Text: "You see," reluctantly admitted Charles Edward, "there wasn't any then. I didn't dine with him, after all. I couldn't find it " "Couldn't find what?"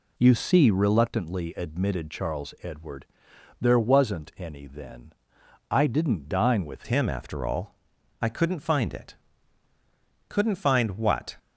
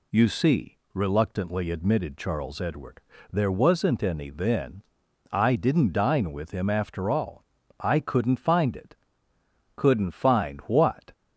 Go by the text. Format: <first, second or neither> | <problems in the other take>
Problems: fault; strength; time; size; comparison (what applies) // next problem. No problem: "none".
second | changes voice at "him"; from 6.8 s on; 4.5 s long